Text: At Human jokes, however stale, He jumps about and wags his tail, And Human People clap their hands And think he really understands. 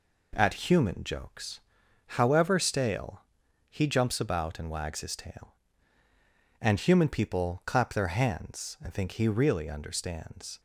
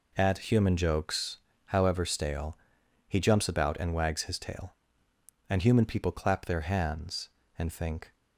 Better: first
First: none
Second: stops before "he really understands"; at 8.1 s

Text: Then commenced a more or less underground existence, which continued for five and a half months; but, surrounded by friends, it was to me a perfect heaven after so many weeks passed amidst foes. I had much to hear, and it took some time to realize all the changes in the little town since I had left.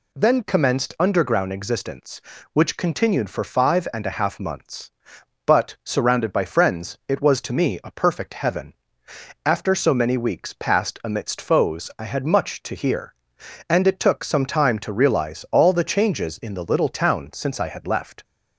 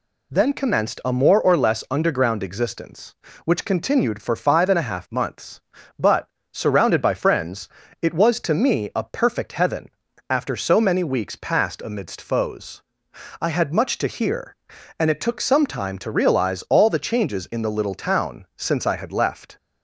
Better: second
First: skips "a more or less"; at 0.9 s // pauses between "heaven" and "after"; noticeable; at 8.7 s; 0.72 s long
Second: pauses between "heaven" and "after"; at 9.8 s; 0.40 s long

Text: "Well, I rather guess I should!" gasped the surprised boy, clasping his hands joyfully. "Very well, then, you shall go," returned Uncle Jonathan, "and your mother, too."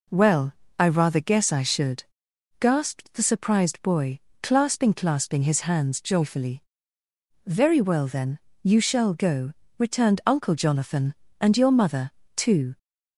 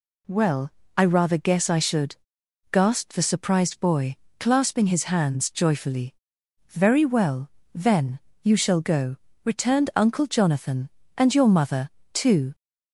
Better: second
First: says "clasping" twice; at 4.9 s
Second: none

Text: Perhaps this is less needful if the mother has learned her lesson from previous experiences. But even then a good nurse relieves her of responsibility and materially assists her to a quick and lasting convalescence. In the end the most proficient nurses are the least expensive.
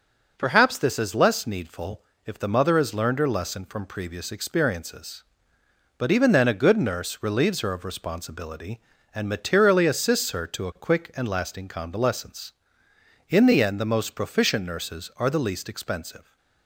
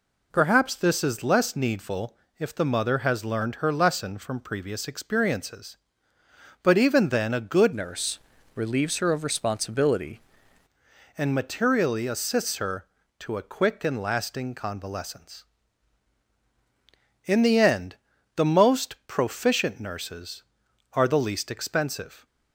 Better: first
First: pauses between "needful" and "if"; slight; at 2.0 s; 0.24 s long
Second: pauses between "needful" and "if"; slight; at 2.1 s; 0.24 s long // changes voice from "nurse" to "responsibility"; from 7.7 to 10.1 s; 2.4 s long // pauses between "nurse" and "relieves"; slight; at 8.1 s; 0.36 s long // pauses between "end" and "the"; at 17.9 s; 0.40 s long

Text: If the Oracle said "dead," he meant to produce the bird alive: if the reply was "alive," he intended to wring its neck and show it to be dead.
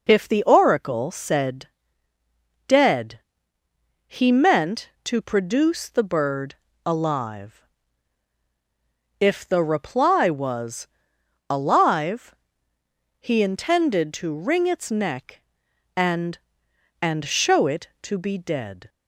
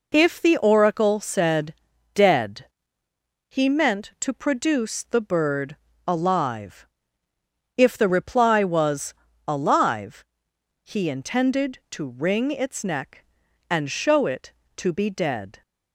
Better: second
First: pauses between "said" and "dead"; noticeable; at 1.6 s; 0.98 s long // pauses between "bird" and "alive"; slight; at 6.5 s; 0.30 s long // pauses between "was" and "alive"; noticeable; at 10.8 s; 0.62 s long // says "and" twice; at 17.0 s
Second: pauses between "said" and "dead"; at 1.7 s; 0.40 s long // pauses between "bird" and "alive"; slight; at 5.7 s; 0.30 s long // pauses between "was" and "alive"; slight; at 9.1 s; 0.32 s long

